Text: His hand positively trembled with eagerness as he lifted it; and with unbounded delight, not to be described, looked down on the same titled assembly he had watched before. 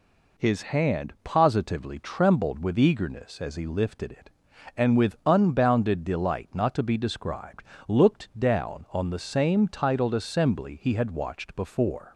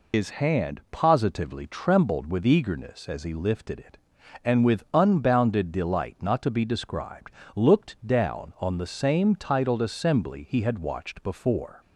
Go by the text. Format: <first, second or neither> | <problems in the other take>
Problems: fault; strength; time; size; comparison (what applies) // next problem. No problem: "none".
first | loses the start of "His"; at 0.1 s; 75 ms